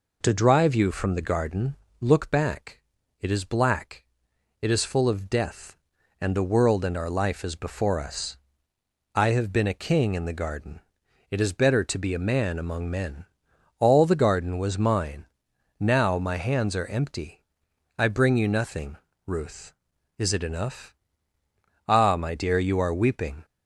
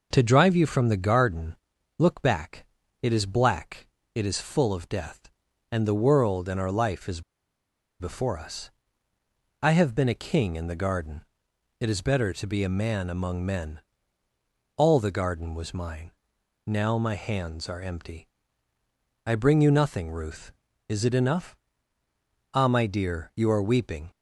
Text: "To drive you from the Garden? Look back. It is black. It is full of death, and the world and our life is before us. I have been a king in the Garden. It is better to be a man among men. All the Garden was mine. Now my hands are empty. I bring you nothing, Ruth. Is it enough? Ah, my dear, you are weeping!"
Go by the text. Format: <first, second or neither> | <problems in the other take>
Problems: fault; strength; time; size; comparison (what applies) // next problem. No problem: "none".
first | pauses between "is" and "before"; noticeable; at 7.2 s; 0.78 s long